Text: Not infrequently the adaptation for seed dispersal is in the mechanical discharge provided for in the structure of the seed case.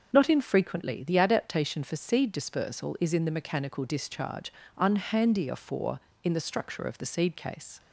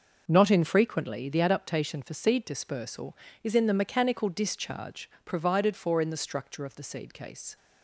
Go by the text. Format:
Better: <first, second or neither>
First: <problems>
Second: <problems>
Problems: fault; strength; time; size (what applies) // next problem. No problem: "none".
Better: second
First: starts louder than the rest; until 1.1 s; 6.5 dB // says "unhandier" for "provided"; at 4.7 s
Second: none